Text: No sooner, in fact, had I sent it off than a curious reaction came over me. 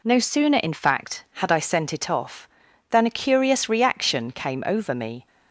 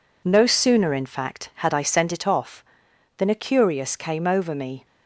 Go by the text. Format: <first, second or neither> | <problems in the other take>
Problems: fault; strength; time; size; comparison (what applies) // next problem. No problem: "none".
first | skips "reaction"; at 3.9 s